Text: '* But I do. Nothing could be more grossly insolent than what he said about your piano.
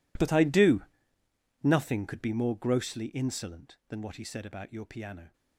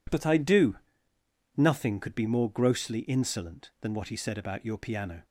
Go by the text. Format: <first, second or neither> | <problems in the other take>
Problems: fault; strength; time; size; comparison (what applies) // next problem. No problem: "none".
second | gets quieter; strong; throughout; 19 dB